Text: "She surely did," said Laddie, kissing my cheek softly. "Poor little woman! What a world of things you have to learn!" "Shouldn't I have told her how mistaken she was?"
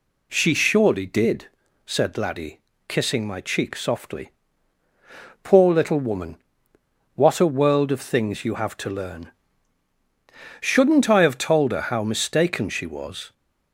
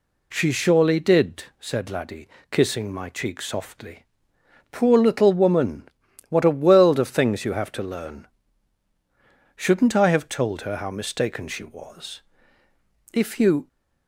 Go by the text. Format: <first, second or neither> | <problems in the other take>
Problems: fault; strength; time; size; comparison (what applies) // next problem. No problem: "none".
first | goes on to say "If you"; from 13.1 s on; 0.56 s long